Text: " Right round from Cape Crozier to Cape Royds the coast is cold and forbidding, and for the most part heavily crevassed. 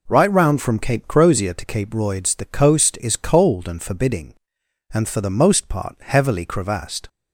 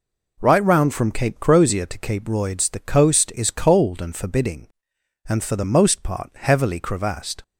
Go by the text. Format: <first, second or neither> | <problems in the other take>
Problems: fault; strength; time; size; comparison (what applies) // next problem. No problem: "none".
neither | none